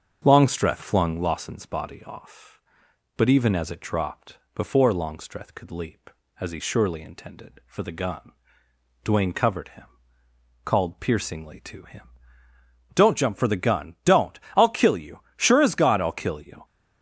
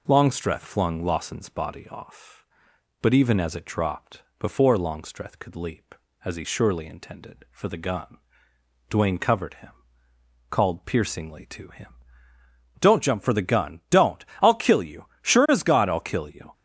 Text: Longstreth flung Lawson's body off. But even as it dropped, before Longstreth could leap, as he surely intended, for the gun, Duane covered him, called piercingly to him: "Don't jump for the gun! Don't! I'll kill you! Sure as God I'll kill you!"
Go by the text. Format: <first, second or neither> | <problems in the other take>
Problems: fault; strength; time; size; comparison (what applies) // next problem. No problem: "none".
second | starts louder than the rest; until 1.2 s; 7 dB